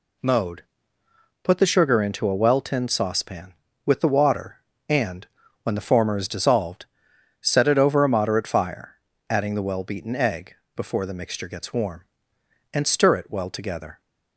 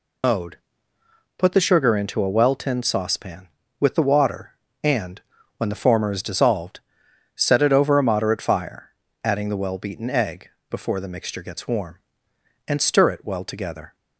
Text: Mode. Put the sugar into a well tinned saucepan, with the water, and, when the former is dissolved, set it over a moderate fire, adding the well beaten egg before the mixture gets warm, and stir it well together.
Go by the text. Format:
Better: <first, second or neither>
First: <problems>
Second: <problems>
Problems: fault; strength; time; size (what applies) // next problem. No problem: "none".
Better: first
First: pauses between "egg" and "before"; slight; at 10.5 s; 0.18 s long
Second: loses the start of "Mode"; at 0.2 s; 95 ms // pauses between "egg" and "before"; slight; at 10.5 s; 0.18 s long